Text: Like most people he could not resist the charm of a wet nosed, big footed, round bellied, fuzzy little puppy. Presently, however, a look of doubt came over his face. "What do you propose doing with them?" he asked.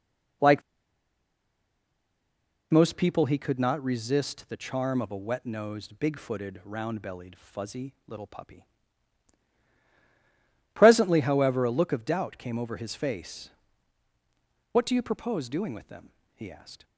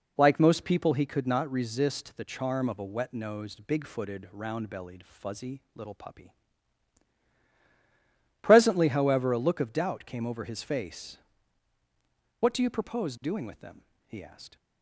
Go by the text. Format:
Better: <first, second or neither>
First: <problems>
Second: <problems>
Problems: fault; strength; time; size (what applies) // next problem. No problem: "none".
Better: second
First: pauses between "Like" and "most"; strong; at 0.6 s; 2.1 s long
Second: none